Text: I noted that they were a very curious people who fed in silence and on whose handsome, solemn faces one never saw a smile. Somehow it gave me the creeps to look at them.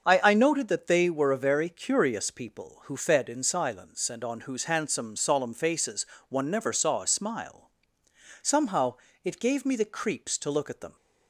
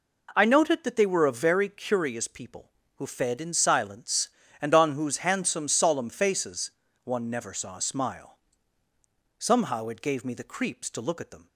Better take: second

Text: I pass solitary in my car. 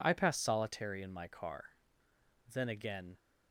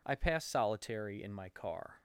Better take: second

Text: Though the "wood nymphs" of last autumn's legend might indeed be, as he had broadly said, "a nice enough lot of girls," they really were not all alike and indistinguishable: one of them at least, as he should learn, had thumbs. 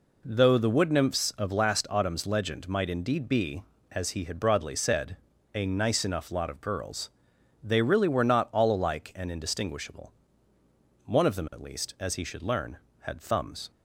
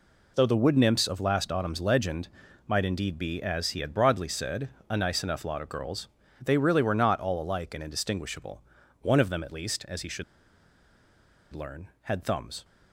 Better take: first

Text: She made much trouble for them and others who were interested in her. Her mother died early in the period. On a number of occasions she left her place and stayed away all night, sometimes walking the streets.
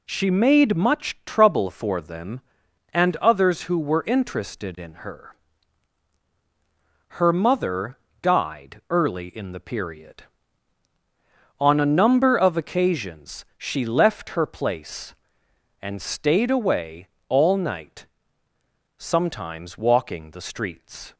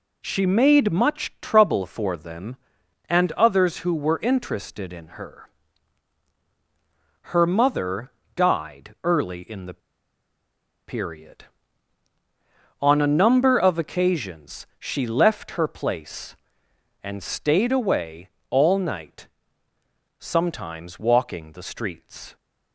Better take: first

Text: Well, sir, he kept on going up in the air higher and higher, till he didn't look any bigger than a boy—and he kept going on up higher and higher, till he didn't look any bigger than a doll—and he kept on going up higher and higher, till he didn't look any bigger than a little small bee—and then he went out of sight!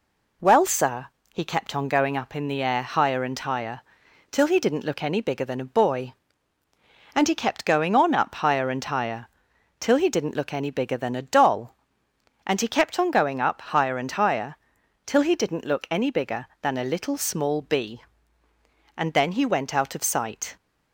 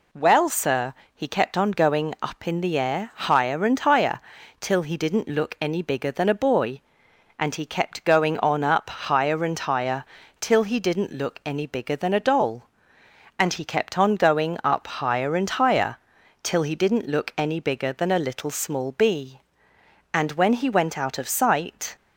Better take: first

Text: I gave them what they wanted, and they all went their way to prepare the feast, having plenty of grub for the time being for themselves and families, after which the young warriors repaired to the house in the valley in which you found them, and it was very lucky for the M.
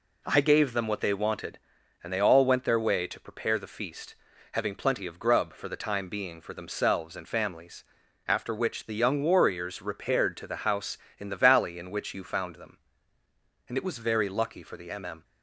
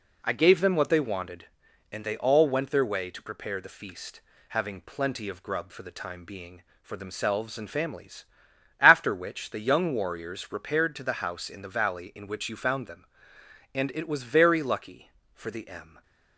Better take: second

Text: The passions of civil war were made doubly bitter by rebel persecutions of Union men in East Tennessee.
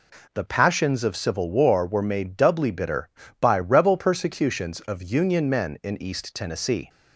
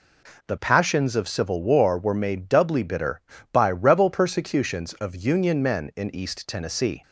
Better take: neither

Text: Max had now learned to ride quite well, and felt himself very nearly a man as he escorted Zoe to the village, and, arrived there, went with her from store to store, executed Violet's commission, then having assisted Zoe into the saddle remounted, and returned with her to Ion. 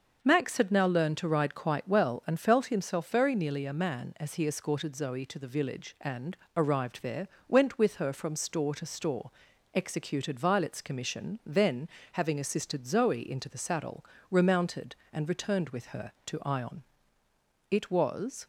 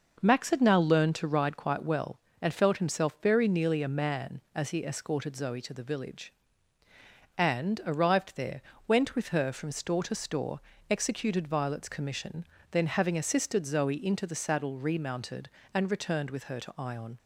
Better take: second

